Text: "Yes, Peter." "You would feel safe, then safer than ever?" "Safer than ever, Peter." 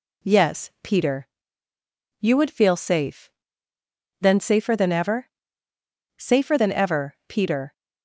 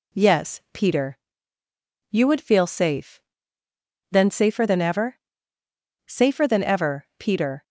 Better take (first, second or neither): neither